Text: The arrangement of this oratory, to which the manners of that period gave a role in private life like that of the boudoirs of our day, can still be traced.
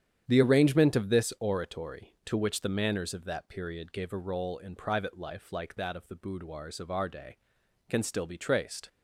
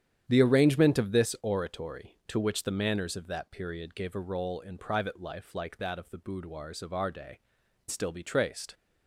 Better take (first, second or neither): first